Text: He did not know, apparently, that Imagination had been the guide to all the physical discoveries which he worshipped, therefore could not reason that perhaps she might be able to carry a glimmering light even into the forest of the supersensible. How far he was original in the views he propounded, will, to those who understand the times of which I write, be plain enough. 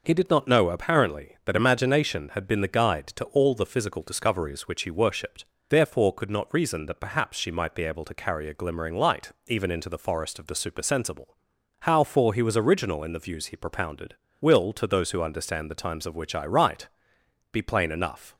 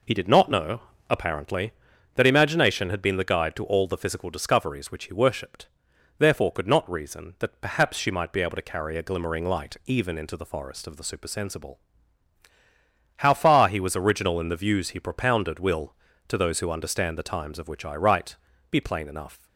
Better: second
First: pauses between "light" and "even"; slight; at 9.3 s; 0.16 s long // says "for" for "far"; at 12.0 s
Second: none

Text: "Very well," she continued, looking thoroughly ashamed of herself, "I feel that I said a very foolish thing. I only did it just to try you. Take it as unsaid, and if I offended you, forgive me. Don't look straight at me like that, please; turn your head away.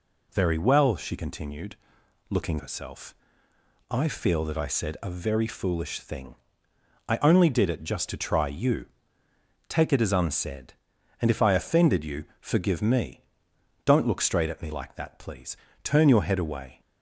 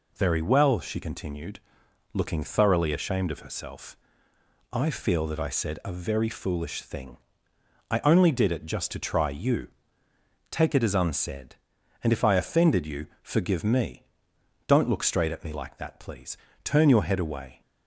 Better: second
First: skips "thoroughly ashamed of"; at 2.5 s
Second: none

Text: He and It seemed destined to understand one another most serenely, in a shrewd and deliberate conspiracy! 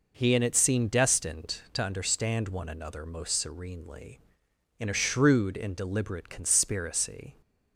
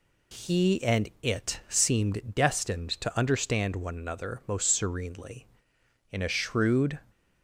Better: first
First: none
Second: stops before "and deliberate conspiracy"; at 7.1 s

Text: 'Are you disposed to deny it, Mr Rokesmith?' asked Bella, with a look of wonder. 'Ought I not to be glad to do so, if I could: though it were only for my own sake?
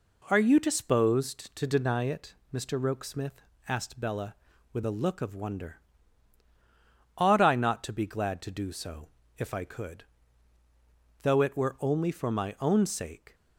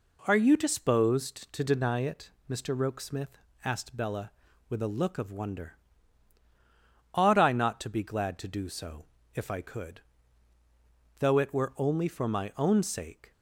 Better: neither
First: none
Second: none

